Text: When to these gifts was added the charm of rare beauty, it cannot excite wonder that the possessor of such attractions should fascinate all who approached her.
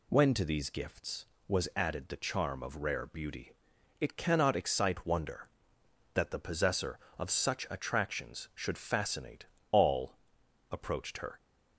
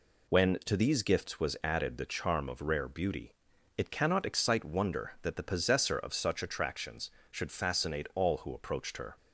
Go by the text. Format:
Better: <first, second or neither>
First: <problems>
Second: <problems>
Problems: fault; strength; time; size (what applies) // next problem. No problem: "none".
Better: second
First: pauses between "fascinate" and "all"; slight; at 9.4 s; 0.24 s long // skips "who"; at 10.4 s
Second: none